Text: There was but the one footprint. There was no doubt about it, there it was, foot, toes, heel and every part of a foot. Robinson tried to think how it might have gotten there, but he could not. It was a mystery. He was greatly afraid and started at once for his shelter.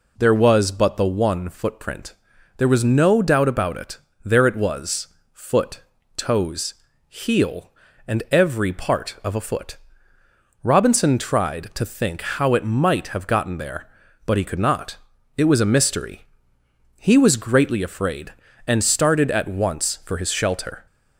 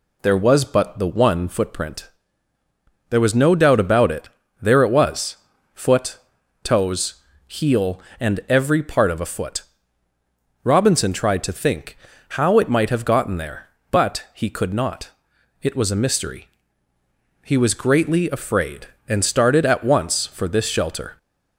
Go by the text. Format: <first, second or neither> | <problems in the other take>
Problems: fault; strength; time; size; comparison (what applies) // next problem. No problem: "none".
first | pauses between "think" and "how"; slight; at 11.9 s; 0.34 s long // says "this" for "his"; at 20.4 s